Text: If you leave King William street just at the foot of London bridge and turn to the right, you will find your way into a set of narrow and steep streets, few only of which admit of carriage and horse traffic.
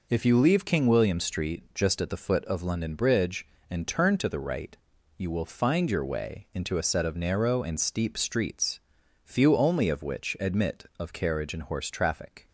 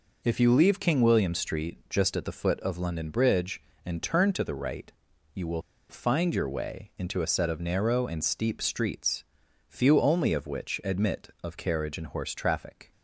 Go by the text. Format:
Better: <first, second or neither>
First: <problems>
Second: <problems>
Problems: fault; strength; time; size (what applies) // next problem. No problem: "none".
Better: first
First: none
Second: pauses between "will" and "find"; slight; at 5.6 s; 0.27 s long